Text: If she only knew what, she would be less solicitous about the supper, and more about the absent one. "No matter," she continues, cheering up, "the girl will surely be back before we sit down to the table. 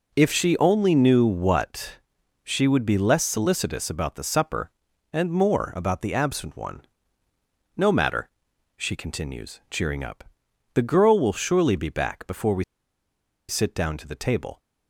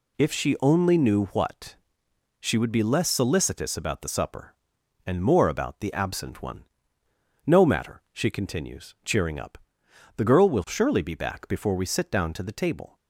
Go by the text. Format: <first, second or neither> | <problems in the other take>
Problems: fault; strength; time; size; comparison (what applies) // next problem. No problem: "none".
second | pauses between "we" and "sit"; noticeable; at 12.6 s; 0.86 s long